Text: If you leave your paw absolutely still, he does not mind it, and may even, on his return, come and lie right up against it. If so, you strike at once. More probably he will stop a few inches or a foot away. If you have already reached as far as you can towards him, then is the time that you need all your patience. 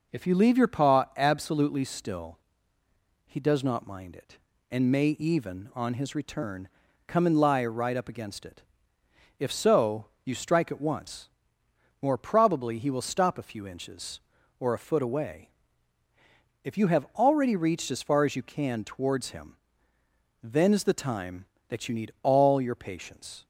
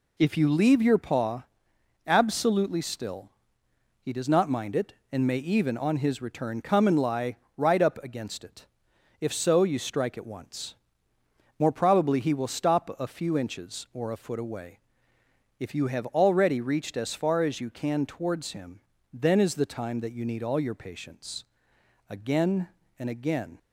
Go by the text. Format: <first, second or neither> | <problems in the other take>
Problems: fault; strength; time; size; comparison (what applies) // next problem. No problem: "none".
first | pauses between "paw" and "absolutely"; noticeable; at 1.4 s; 0.60 s long // pauses between "lie" and "right"; slight; at 7.3 s; 0.20 s long // goes on to say "Again and again"; from 22.0 s on; 1.4 s long